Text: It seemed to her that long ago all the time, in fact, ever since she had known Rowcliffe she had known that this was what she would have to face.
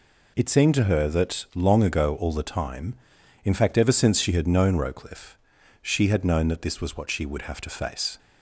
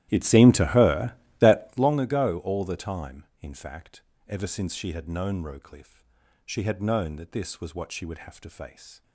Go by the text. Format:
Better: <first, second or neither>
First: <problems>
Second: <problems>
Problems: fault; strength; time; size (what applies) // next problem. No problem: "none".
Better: first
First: pauses between "Rowcliffe" and "she"; noticeable; at 5.3 s; 0.48 s long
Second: starts louder than the rest; strong; until 2.0 s; 13.5 dB // pauses between "Rowcliffe" and "she"; at 6.0 s; 0.44 s long